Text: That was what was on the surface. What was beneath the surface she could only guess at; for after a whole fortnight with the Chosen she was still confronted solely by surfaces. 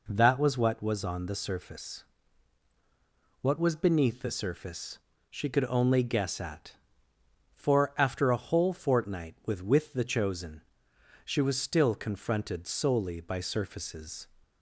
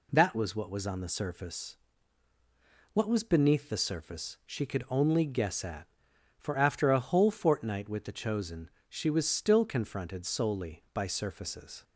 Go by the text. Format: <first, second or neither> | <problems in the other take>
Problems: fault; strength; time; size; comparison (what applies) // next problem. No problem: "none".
second | pauses between "surface" and "she"; slight; at 4.9 s; 0.32 s long // says "with" twice; at 9.6 s // pauses between "Chosen" and "she"; noticeable; at 10.6 s; 0.64 s long; slight in the second